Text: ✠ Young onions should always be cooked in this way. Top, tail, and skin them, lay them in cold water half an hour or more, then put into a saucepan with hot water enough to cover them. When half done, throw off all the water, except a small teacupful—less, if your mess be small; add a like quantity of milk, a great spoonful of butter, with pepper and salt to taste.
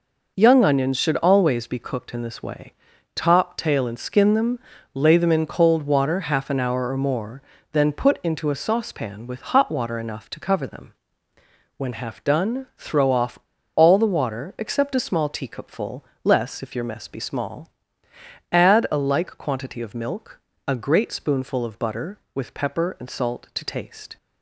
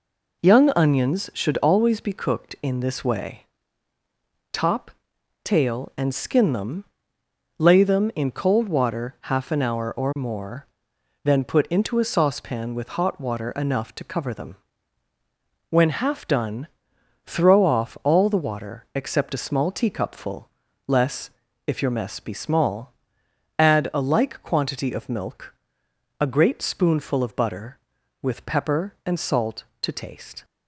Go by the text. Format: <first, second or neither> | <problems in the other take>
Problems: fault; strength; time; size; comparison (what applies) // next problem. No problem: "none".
second | pauses between "off" and "all"; at 13.3 s; 0.38 s long